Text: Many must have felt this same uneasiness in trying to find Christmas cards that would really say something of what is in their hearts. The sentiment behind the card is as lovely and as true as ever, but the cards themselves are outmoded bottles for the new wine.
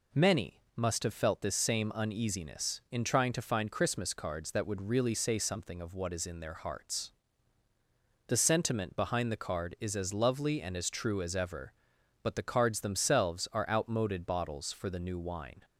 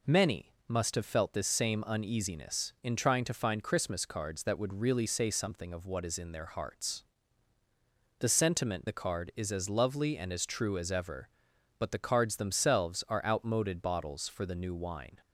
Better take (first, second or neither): first